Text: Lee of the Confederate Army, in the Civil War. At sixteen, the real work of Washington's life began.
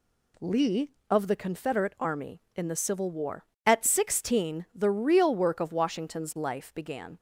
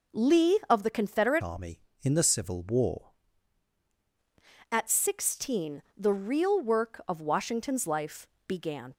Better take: first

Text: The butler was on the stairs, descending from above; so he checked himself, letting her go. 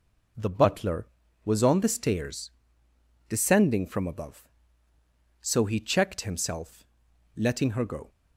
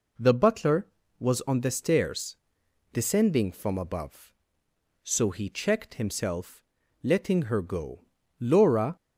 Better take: first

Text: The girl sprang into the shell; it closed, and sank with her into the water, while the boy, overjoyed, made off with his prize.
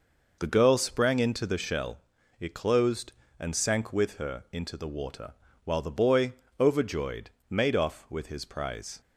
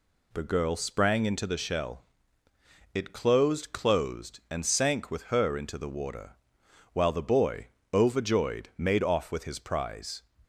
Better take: first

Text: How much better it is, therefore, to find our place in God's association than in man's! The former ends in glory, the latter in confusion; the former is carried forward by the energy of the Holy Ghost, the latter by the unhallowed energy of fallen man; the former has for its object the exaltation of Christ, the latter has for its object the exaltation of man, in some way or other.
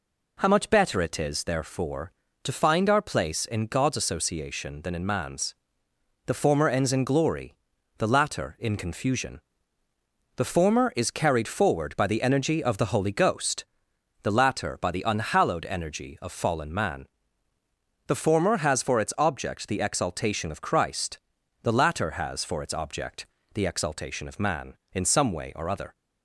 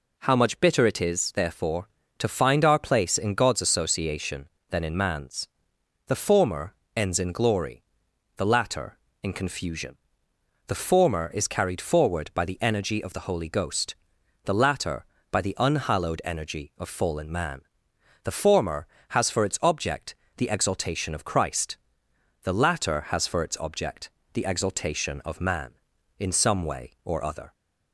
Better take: first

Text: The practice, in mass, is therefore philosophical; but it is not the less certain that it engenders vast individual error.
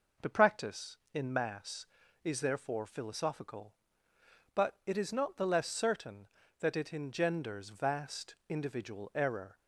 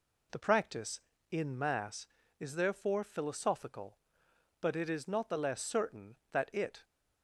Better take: first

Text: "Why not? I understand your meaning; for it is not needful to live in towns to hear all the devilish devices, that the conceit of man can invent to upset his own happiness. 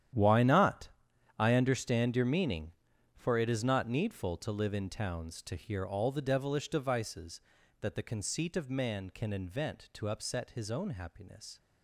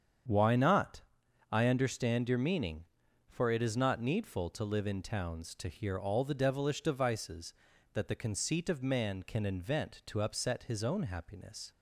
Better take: second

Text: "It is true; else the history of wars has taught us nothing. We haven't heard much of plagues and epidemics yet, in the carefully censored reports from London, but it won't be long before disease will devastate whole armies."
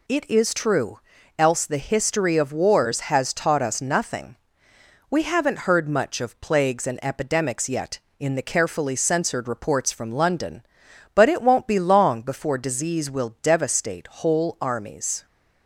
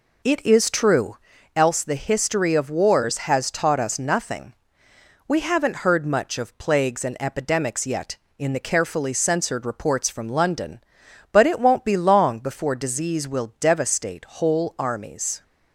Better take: first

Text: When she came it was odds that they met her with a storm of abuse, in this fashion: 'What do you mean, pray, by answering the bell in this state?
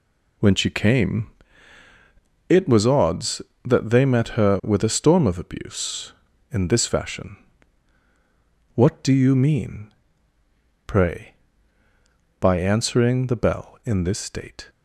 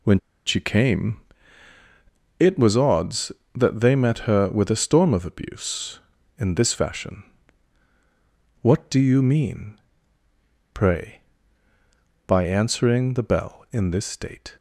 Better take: first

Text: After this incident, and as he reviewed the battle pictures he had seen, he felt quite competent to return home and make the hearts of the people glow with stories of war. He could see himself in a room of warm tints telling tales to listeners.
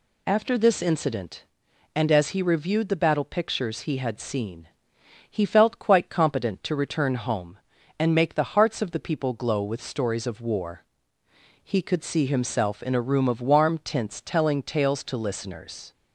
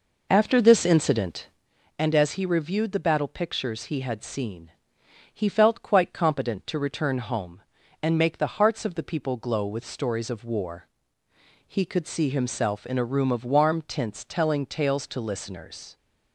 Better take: first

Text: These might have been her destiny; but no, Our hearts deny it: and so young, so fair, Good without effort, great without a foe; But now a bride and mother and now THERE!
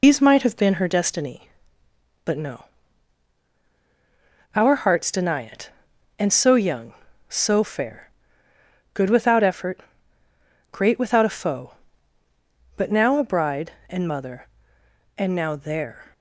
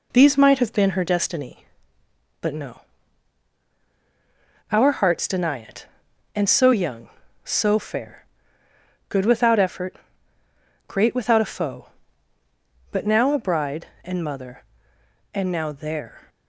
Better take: second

